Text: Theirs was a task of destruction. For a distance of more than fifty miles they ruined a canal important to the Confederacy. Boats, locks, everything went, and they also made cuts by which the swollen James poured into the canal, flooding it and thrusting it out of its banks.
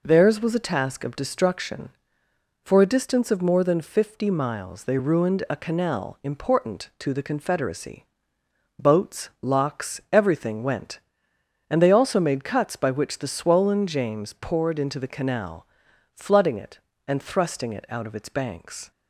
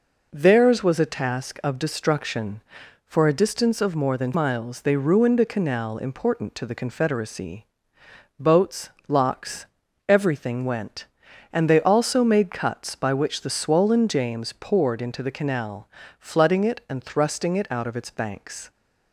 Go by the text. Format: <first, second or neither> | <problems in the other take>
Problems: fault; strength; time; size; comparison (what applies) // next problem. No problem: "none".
first | skips "fifty"; at 4.3 s